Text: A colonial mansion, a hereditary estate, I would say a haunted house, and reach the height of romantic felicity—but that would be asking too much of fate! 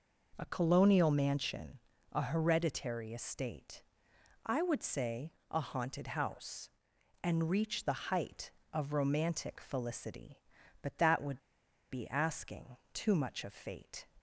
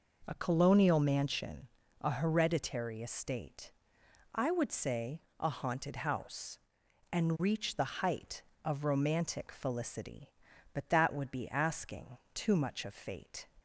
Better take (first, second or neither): second